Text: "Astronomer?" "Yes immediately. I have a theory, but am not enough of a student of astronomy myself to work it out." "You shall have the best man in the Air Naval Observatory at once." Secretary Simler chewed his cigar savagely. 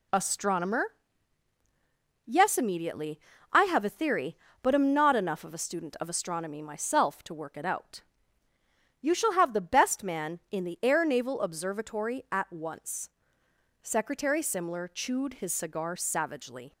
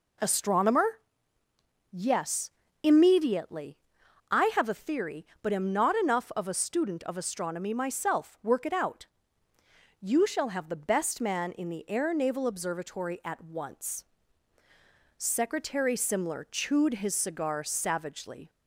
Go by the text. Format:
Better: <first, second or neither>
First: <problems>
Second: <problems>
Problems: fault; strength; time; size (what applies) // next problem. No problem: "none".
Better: first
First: none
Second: pauses between "Yes" and "immediately"; slight; at 2.4 s; 0.32 s long // skips "to"; at 8.4 s